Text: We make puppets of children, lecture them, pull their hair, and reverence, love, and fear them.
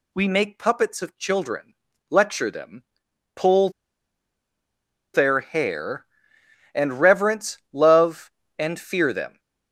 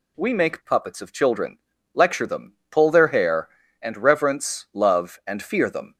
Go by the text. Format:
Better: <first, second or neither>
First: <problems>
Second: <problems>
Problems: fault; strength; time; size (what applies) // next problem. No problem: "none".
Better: second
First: pauses between "pull" and "their"; strong; at 3.6 s; 1.4 s long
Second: none